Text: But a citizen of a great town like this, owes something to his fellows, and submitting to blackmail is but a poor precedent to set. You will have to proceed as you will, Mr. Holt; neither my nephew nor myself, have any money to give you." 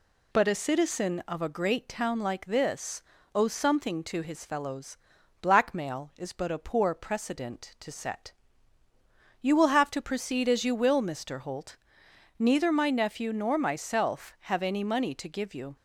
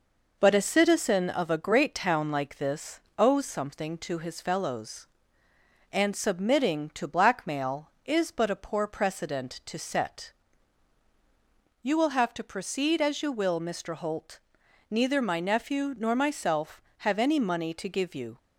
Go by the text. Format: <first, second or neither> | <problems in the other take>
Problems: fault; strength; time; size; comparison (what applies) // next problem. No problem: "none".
second | skips "and submitting to"; at 5.1 s